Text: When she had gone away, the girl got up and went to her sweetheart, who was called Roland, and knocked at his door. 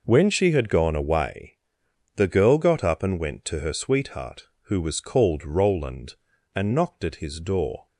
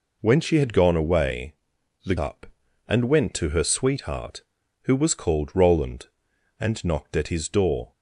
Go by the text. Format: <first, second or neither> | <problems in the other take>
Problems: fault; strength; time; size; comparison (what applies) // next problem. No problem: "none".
first | skips "girl got"; at 2.1 s